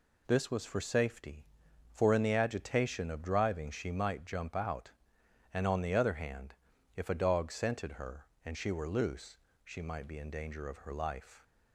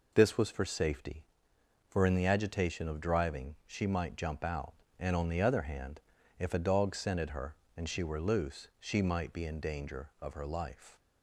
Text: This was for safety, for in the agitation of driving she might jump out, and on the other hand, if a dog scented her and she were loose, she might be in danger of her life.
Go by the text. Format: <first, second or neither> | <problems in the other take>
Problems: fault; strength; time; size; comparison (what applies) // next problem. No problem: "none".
neither | none